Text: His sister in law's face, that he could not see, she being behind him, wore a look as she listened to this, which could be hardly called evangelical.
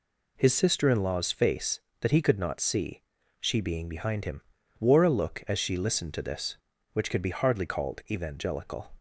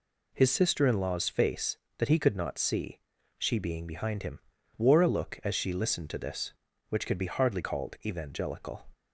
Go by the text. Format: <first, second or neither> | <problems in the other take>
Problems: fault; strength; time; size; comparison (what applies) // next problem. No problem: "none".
neither | none